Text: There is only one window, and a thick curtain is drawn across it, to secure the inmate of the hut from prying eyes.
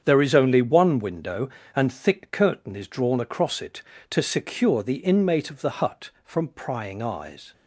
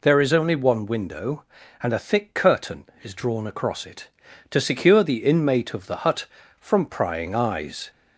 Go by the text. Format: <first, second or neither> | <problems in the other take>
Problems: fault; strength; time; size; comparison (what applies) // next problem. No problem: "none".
second | starts louder than the rest; strong; until 1.0 s; 8 dB // skips "a"; at 1.9 s